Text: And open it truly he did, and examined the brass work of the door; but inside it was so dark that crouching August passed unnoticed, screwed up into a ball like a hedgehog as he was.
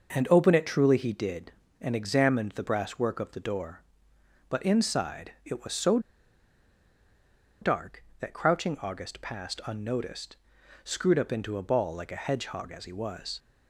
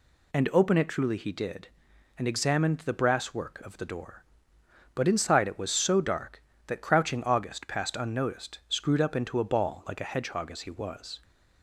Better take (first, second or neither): second